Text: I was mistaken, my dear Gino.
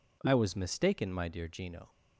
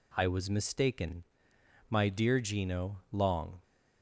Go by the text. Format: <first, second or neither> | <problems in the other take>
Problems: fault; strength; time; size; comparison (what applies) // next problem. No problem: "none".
first | goes on to say "Long"; from 3.1 s on; 0.50 s long